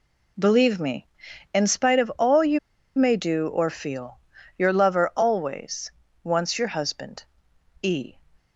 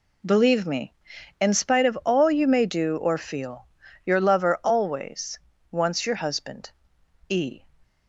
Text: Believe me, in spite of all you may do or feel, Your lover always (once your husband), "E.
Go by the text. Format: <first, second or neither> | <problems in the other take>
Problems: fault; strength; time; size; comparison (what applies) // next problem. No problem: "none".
second | pauses between "you" and "may"; at 2.5 s; 0.39 s long